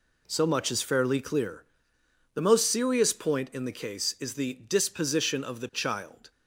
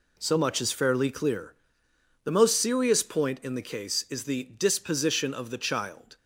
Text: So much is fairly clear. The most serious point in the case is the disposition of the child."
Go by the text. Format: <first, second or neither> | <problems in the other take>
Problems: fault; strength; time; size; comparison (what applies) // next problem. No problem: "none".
neither | none